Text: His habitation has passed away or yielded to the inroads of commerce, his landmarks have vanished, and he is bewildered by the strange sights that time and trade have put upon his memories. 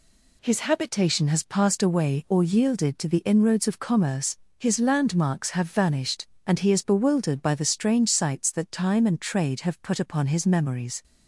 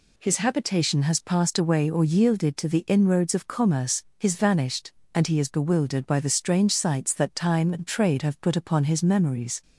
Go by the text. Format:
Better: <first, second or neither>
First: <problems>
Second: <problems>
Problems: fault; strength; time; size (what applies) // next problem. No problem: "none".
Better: first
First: none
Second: skips "landmarks have"; at 4.3 s